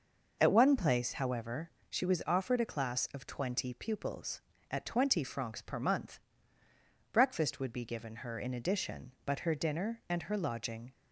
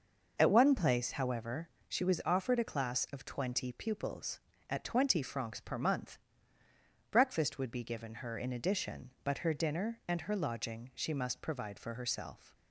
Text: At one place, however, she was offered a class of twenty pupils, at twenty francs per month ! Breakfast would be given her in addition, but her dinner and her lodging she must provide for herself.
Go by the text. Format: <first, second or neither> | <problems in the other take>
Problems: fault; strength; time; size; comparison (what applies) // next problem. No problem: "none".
second | stops before "she must provide for herself"; at 10.9 s